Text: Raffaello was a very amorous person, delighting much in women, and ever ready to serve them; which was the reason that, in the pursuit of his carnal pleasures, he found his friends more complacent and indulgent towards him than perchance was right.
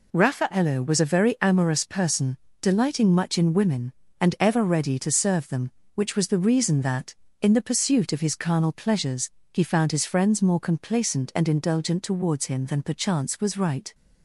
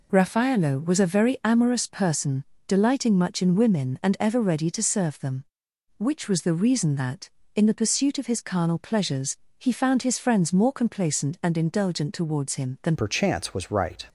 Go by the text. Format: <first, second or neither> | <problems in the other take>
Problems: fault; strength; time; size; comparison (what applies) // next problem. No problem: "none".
first | changes voice at "perchance"; from 12.9 s on; 1.1 s long